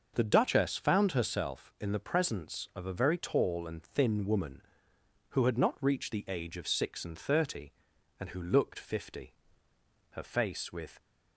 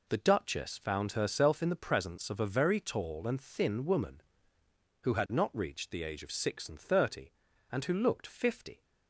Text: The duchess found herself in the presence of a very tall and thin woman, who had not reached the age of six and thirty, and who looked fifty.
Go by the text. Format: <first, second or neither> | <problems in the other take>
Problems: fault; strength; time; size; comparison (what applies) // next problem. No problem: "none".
second | starts louder than the rest; until 1.1 s; 6 dB // goes on to say "Her face with"; noticeable; from 10.1 s on; 0.90 s long